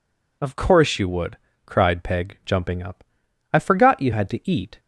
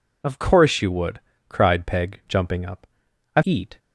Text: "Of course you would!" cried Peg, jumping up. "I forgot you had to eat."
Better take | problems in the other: first | skips "forgot you had to"; at 3.4 s

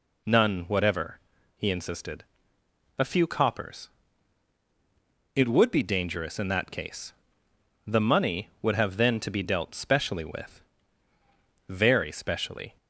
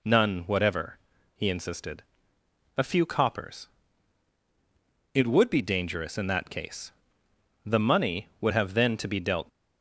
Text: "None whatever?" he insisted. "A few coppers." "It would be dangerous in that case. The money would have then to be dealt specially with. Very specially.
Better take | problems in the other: first | stops before "specially with Very specially"; at 9.4 s

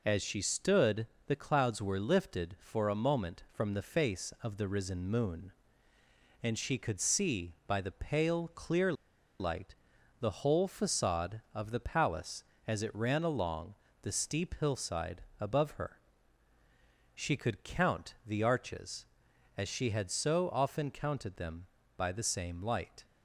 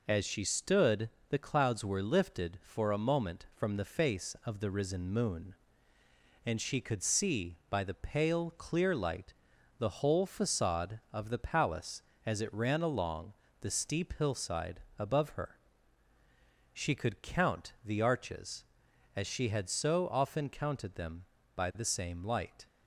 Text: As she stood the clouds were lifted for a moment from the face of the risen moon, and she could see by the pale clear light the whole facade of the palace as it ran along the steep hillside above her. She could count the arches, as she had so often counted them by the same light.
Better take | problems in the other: second | pauses between "stood" and "the"; slight; at 1.0 s; 0.20 s long; slight in the second // pauses between "clear" and "light"; noticeable; at 8.9 s; 0.47 s long // pauses between "light" and "the"; at 9.7 s; 0.44 s long; also in the second // pauses between "along" and "the"; slight; at 13.7 s; 0.28 s long; slight in the second // pauses between "hillside" and "above"; slight; at 15.2 s; 0.16 s long; slight in the second

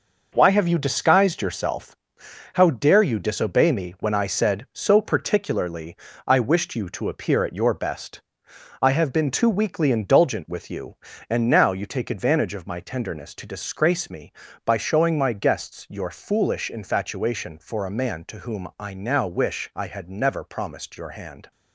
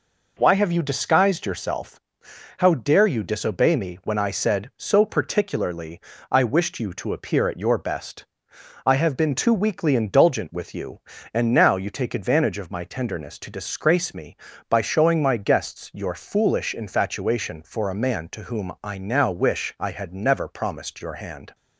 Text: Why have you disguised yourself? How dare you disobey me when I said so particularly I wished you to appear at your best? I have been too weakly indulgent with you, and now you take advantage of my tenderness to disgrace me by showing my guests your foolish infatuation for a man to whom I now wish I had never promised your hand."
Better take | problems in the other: second | gets quieter; strong; throughout; 7.5 dB // pauses between "particularly" and "I"; slight; at 5.9 s; 0.32 s long; slight in the second

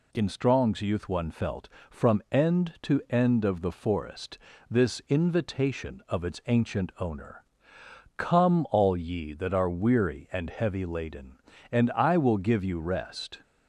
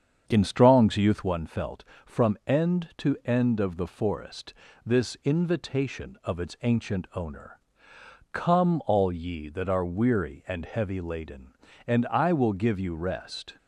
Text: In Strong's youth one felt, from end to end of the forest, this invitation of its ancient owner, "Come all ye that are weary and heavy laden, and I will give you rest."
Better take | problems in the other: first | starts louder than the rest; strong; until 1.4 s; 7 dB

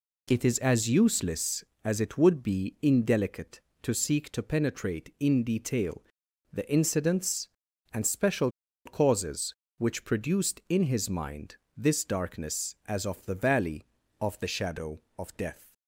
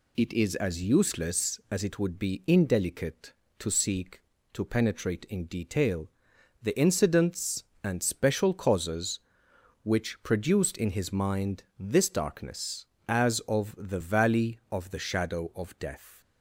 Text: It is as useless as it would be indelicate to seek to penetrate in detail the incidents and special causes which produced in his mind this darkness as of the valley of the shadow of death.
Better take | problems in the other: second | pauses between "detail" and "the"; noticeable; at 6.0 s; 0.50 s long; noticeable in the second // pauses between "special" and "causes"; slight; at 8.5 s; 0.34 s long // pauses between "mind" and "this"; slight; at 11.5 s; 0.18 s long

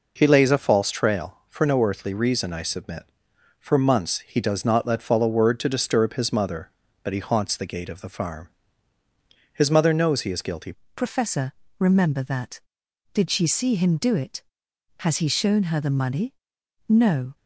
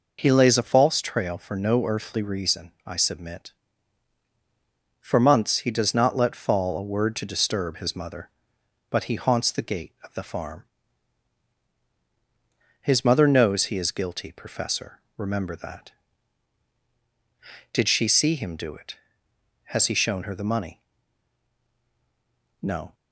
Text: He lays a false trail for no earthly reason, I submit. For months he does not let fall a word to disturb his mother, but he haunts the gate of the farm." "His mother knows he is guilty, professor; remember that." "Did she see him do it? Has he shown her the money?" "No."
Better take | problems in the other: second | changes voice at "professor"; from 10.9 s on; 6.4 s long

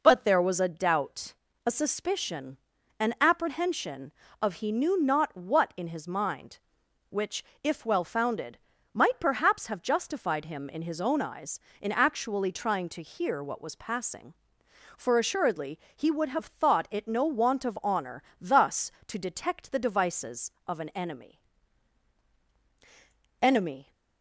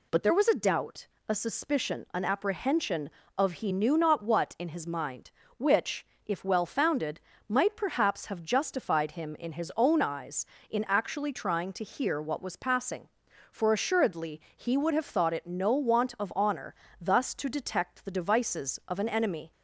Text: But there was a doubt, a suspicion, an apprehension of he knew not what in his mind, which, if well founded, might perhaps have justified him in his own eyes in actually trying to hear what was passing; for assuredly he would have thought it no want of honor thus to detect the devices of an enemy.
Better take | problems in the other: second | pauses between "assuredly" and "he"; slight; at 15.7 s; 0.16 s long; slight in the second // pauses between "honor" and "thus"; slight; at 18.2 s; 0.18 s long; slight in the second // says "enemy" twice; at 23.4 s

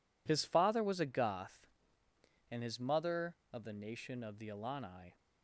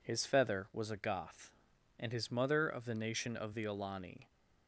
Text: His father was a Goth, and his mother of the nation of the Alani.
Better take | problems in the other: first | says "feather" for "father"; at 0.2 s

